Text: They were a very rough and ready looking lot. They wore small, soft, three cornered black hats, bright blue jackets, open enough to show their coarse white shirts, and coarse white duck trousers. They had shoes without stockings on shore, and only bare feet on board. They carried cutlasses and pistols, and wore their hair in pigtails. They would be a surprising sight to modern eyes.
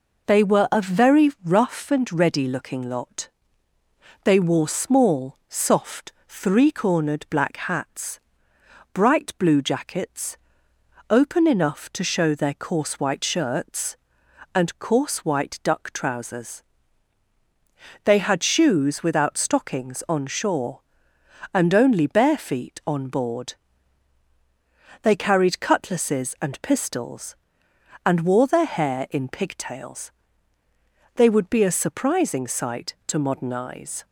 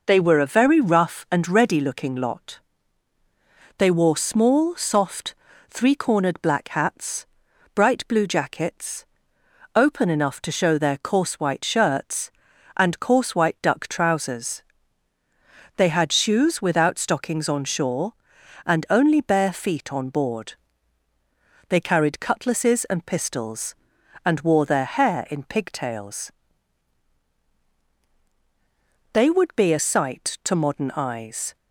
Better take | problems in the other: first | skips "surprising"; at 29.7 s

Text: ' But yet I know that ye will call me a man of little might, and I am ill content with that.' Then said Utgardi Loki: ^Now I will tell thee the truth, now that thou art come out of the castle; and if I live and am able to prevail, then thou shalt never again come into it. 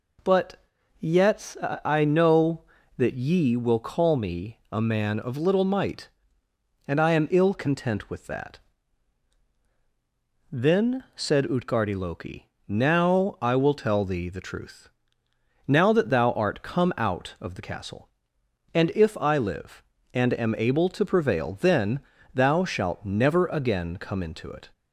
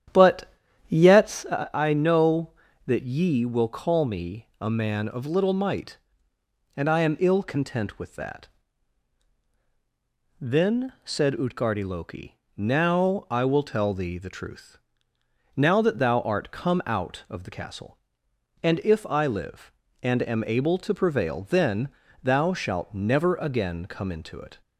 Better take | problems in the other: first | starts louder than the rest; strong; until 1.7 s; 10 dB // pauses between "But" and "yet"; slight; at 0.5 s; 0.36 s long; slight in the first // pauses between "yet" and "I"; slight; at 1.4 s; 0.26 s long; slight in the first // pauses between "then" and "thou"; slight; at 21.9 s; 0.32 s long; slight in the first

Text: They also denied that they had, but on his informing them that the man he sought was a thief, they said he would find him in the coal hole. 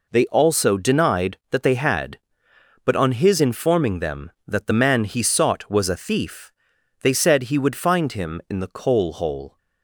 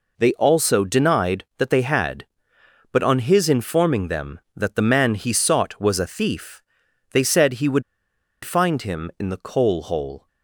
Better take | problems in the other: first | pauses between "would" and "find"; noticeable; at 7.8 s; 0.61 s long

